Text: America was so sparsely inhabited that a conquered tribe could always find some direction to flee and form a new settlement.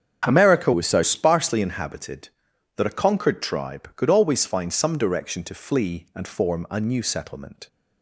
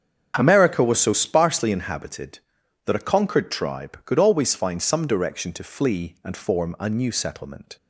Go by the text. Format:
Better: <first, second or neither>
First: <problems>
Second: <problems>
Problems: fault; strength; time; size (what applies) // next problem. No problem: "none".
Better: second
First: starts louder than the rest; strong; until 1.2 s; 8 dB // changes voice from "was" to "so"; from 0.7 to 1.0 s; 0.3 s long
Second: starts louder than the rest; strong; until 1.3 s; 7.5 dB